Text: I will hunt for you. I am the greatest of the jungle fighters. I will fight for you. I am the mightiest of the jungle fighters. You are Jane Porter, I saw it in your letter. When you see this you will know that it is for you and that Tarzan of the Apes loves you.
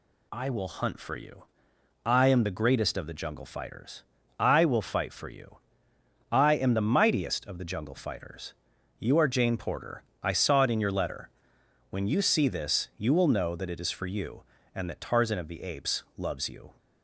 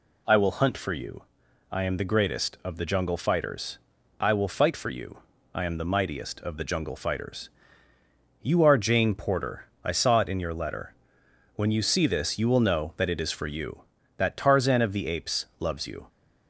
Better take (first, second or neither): first